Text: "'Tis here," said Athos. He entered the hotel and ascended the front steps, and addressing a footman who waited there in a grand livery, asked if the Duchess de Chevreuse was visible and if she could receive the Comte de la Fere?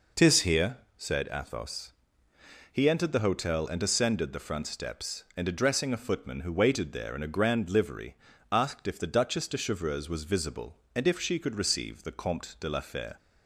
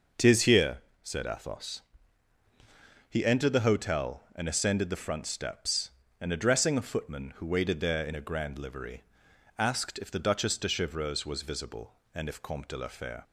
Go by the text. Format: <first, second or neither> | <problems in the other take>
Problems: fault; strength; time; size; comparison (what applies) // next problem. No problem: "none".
first | skips "she could receive the"; at 12.4 s